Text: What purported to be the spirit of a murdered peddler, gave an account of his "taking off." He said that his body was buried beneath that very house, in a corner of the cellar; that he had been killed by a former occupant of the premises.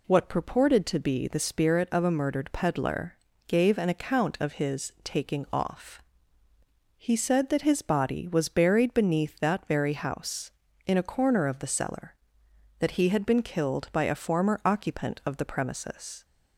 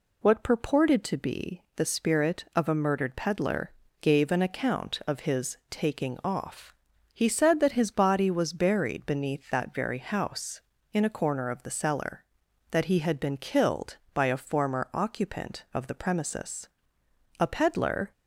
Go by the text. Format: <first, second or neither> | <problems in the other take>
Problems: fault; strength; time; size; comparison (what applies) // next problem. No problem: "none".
first | pauses between "be" and "the"; slight; at 1.6 s; 0.15 s long // goes on to say "A peddler"; noticeable; from 17.3 s on; 0.72 s long